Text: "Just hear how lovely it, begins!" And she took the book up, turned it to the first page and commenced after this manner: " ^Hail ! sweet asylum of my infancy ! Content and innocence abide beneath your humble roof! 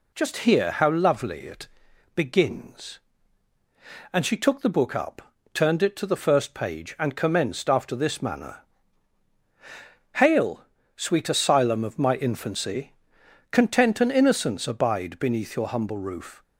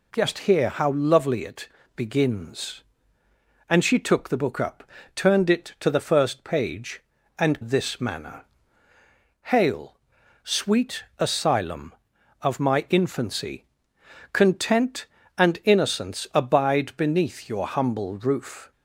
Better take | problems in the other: first | skips "commenced after"; at 7.6 s

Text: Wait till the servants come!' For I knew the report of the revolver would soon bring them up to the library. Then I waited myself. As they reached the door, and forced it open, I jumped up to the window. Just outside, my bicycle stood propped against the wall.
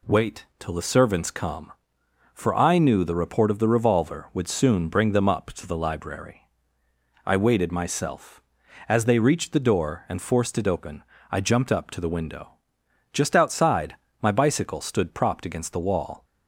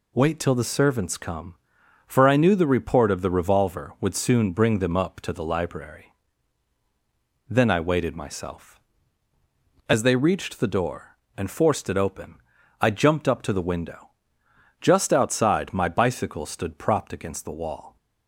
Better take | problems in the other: second | pauses between "Wait" and "till"; slight; at 0.4 s; 0.16 s long // skips "Then"; at 6.8 s

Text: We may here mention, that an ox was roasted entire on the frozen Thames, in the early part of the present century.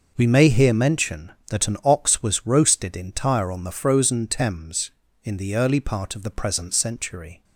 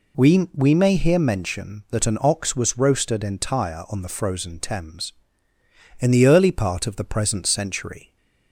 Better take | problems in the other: first | says "We" twice; at 0.5 s

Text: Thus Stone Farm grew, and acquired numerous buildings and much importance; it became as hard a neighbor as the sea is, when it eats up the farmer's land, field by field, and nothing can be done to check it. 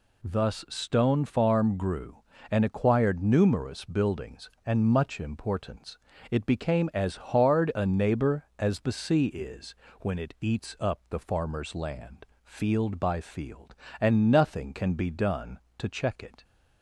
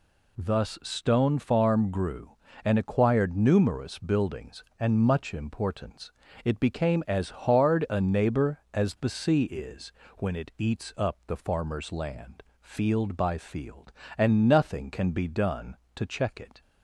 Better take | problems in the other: neither | none

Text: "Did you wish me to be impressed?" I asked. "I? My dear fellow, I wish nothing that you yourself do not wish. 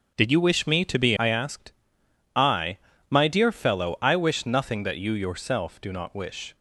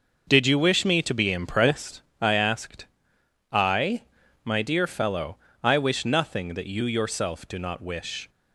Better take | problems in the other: second | starts louder than the rest; until 1.1 s; 6.5 dB; noticeable in the second // skips "impressed"; at 1.1 s

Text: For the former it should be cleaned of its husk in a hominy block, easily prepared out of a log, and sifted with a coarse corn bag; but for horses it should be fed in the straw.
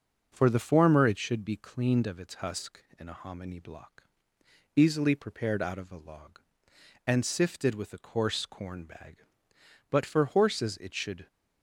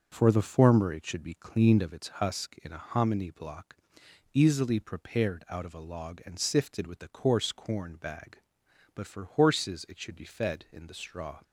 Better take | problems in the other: second | stops before "be fed in the straw"; at 11.2 s

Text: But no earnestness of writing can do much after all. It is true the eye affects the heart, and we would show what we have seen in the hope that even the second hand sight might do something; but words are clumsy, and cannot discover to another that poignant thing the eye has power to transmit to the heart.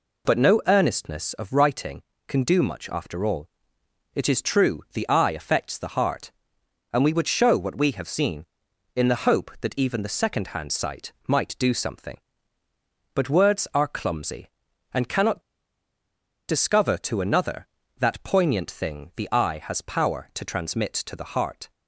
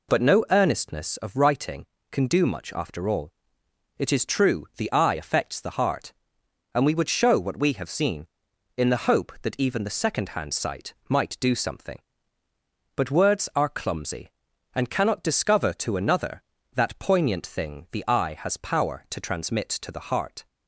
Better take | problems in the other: second | pauses between "sight" and "might"; slight; at 11.1 s; 0.16 s long; slight in the second // pauses between "cannot" and "discover"; at 15.4 s; 1.0 s long

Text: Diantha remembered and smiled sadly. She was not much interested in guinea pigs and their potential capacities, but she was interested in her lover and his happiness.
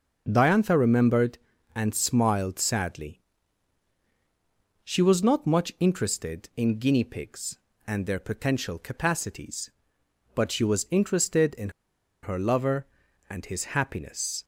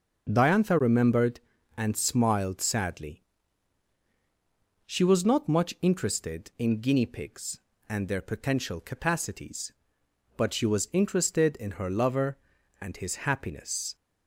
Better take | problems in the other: second | starts louder than the rest; until 1.2 s; 6 dB // pauses between "in" and "her"; noticeable; at 11.6 s; 0.53 s long

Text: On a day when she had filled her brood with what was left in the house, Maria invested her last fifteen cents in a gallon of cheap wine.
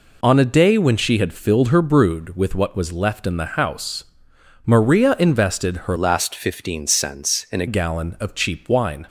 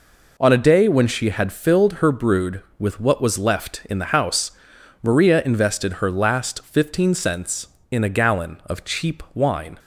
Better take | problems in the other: second | changes voice from "last" to "a"; from 5.9 to 7.6 s; 1.7 s long

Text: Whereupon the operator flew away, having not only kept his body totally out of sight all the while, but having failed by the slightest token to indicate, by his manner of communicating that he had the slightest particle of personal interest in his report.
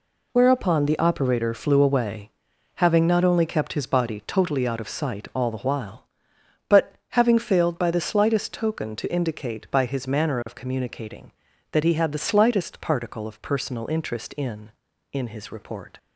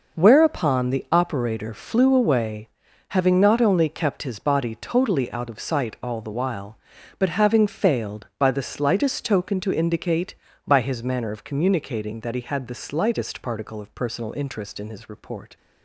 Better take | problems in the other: second | pauses between "but" and "having"; slight; at 6.9 s; 0.18 s long // says "in" twice; at 15.1 s

